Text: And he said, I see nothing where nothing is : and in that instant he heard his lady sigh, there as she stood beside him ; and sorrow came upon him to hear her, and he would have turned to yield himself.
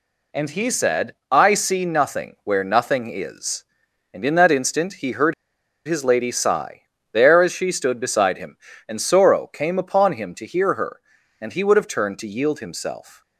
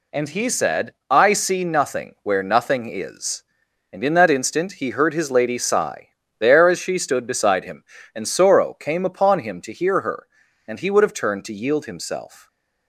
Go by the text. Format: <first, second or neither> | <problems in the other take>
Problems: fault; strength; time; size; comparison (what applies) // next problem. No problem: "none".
second | pauses between "heard" and "his"; noticeable; at 5.3 s; 0.52 s long